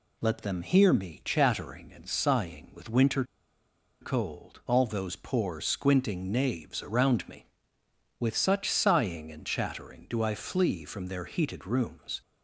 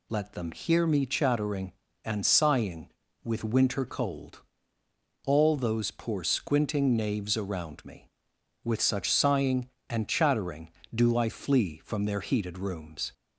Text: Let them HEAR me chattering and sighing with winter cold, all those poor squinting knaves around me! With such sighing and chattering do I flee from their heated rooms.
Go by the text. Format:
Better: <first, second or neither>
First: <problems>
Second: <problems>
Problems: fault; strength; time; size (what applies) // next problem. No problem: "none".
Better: second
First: pauses between "winter" and "cold"; noticeable; at 3.2 s; 0.78 s long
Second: none